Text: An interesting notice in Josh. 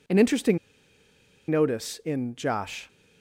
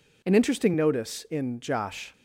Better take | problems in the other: second | pauses between "interesting" and "notice"; noticeable; at 0.5 s; 0.91 s long

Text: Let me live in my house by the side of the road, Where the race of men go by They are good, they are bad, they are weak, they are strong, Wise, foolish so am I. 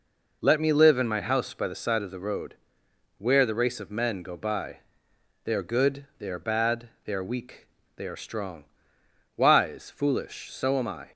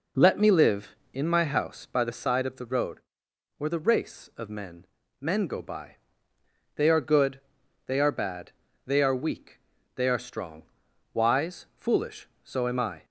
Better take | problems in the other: first | says "men" twice; at 5.2 s // pauses between "by" and "They"; noticeable; at 5.9 s; 0.80 s long; noticeable in the first

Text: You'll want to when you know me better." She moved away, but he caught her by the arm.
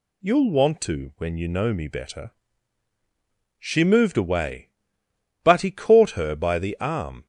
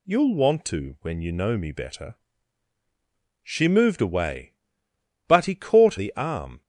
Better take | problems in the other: first | skips "her by"; at 5.9 s

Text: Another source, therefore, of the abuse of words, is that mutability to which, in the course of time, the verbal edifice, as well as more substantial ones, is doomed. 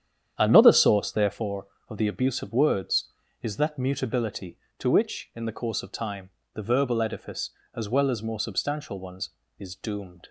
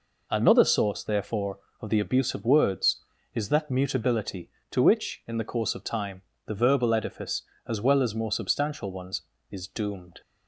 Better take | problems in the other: second | starts louder than the rest; strong; until 1.4 s; 9 dB

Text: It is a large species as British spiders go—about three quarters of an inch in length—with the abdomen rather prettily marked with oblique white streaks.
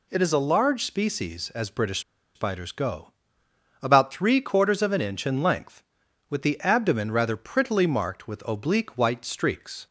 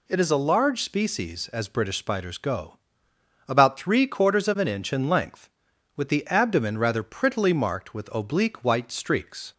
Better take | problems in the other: second | pauses between "British" and "spiders"; slight; at 1.9 s; 0.35 s long

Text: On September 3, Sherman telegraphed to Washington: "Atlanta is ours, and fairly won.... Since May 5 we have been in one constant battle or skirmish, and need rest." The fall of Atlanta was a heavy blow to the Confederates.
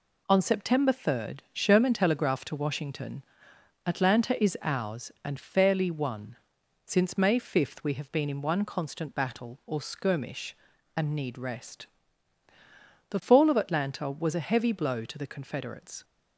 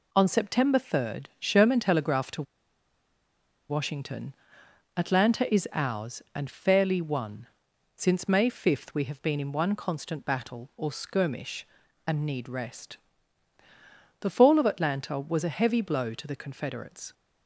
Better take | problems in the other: first | pauses between "to" and "Washington"; strong; at 2.4 s; 1.2 s long

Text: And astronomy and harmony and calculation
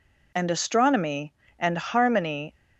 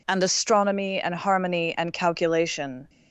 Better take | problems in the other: second | stops before "and calculation"; at 2.5 s

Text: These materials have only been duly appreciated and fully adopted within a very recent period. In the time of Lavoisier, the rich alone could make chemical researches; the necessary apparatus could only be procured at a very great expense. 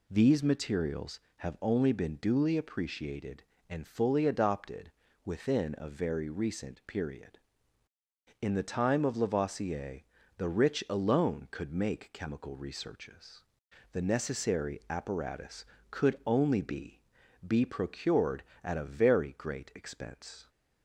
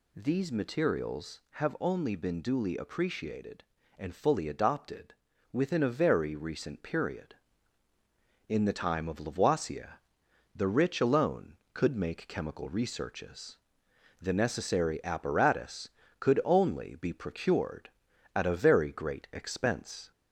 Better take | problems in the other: second | pauses between "adopted" and "within"; slight; at 4.9 s; 0.32 s long; also in the second // says "be" twice; at 17.4 s

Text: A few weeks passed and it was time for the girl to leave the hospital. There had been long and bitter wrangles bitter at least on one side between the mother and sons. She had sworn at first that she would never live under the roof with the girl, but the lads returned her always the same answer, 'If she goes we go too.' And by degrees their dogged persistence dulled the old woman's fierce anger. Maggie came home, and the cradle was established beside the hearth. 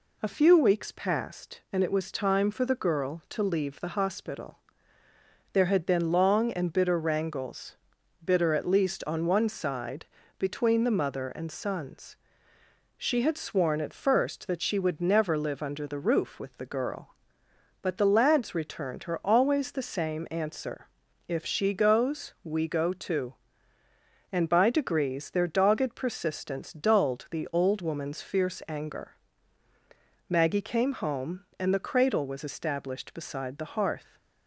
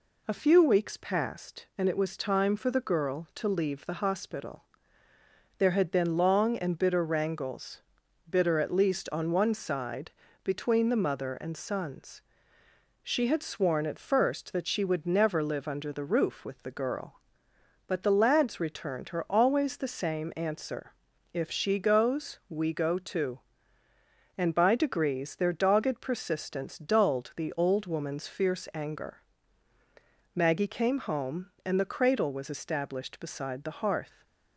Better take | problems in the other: neither | pauses between "wrangles" and "bitter"; noticeable; the same in both // pauses between "side" and "between"; slight; the same in both

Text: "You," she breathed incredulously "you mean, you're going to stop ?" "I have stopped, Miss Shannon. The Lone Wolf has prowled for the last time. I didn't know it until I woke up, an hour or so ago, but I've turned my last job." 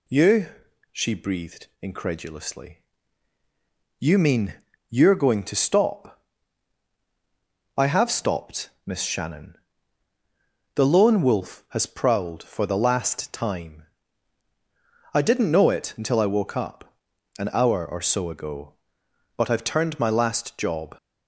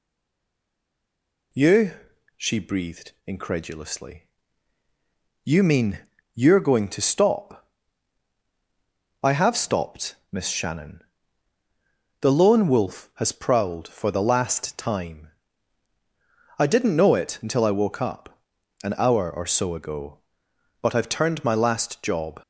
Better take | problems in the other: first | stays silent before the first word; noticeable; until 1.5 s; 1.5 s long // pauses between "incredulously" and "you"; at 4.2 s; 1.2 s long; also in the first

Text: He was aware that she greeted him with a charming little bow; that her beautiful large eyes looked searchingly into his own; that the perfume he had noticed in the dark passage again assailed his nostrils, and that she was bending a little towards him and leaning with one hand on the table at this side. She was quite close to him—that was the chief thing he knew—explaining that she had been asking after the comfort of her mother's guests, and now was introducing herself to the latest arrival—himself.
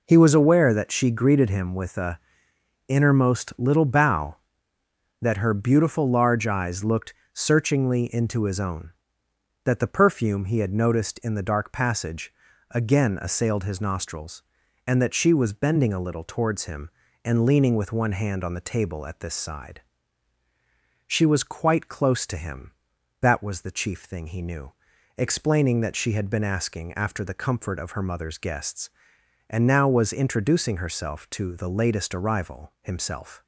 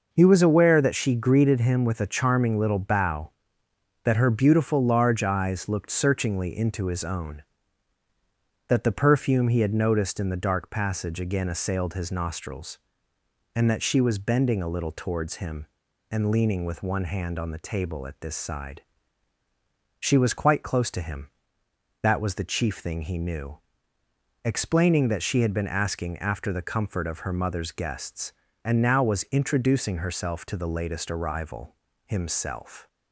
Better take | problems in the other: second | says "innermost" for "charming"; at 2.8 s // pauses between "looked" and "searchingly"; slight; at 7.1 s; 0.20 s long // pauses between "passage" and "again"; at 12.3 s; 0.38 s long

